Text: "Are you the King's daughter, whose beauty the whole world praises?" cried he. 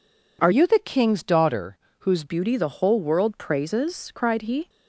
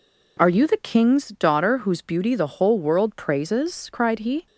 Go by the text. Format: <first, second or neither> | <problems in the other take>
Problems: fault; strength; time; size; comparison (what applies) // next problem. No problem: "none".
second | changes voice from "you" to "whose"; from 0.5 to 2.2 s; 1.7 s long